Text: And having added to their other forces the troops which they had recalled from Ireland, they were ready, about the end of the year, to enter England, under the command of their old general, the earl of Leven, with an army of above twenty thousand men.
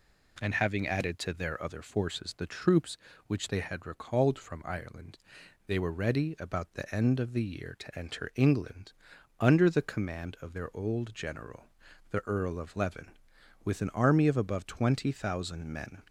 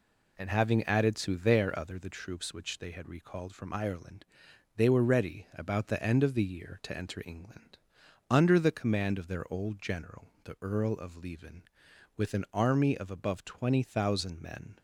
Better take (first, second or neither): first